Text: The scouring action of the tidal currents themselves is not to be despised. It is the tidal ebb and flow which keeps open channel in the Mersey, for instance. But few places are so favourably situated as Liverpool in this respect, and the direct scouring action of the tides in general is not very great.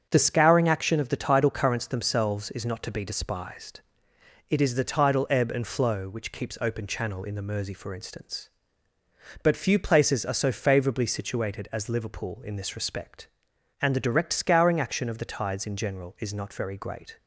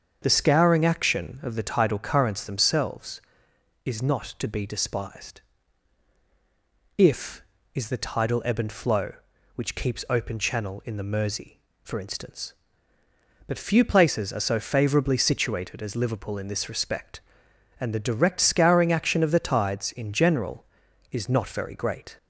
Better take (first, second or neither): first